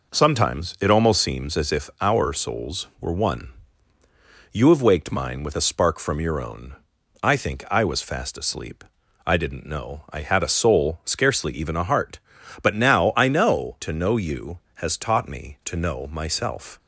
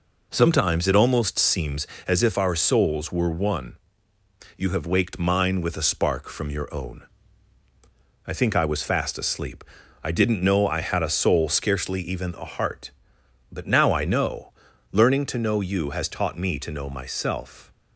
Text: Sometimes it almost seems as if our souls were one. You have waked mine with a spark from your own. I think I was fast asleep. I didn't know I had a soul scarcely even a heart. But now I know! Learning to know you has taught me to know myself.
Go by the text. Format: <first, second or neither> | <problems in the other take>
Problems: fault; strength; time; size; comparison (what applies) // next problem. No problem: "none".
second | skips "Learning"; at 13.7 s